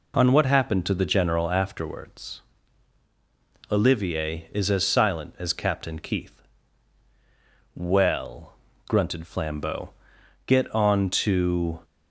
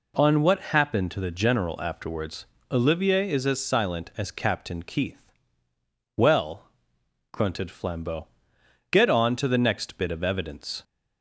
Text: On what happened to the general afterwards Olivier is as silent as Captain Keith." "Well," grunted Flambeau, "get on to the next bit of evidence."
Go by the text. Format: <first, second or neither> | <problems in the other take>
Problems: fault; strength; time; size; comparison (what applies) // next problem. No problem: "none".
second | pauses between "afterwards" and "Olivier"; strong; at 2.4 s; 1.2 s long; slight in the second // stops before "the next bit of evidence"; at 11.8 s